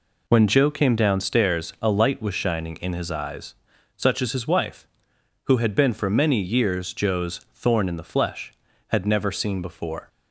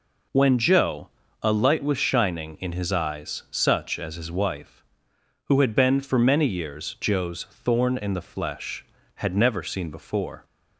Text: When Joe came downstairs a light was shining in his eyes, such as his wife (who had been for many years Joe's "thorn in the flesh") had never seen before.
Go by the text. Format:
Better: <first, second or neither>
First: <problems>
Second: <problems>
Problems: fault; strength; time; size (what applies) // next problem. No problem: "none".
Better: first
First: none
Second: skips "came downstairs"; at 1.2 s